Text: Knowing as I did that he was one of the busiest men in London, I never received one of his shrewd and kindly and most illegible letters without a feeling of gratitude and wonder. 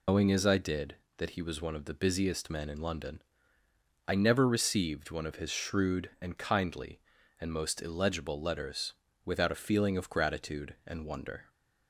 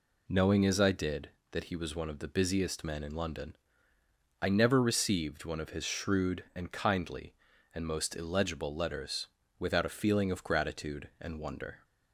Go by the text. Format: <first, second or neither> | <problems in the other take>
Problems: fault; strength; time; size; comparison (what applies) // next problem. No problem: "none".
second | loses the start of "Knowing"; at 0.0 s; 140 ms // pauses between "letters" and "without"; slight; at 8.9 s; 0.32 s long; slight in the second